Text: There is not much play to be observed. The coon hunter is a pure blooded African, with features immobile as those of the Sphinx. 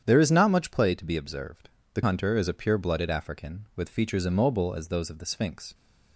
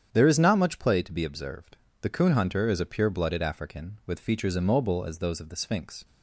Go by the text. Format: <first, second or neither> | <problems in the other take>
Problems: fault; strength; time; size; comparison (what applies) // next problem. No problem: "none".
second | starts louder than the rest; strong; until 1.0 s; 9 dB; strong in the second // skips "coon"; at 2.0 s